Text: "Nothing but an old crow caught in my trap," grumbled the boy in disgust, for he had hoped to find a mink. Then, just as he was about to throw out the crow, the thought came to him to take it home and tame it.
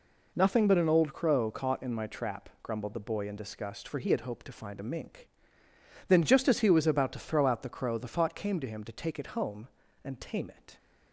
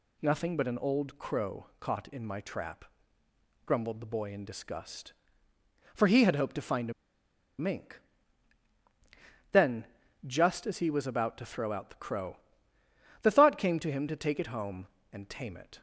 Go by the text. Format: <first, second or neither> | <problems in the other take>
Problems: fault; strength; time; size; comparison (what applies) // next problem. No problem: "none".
first | pauses between "a" and "mink"; noticeable; at 6.9 s; 0.67 s long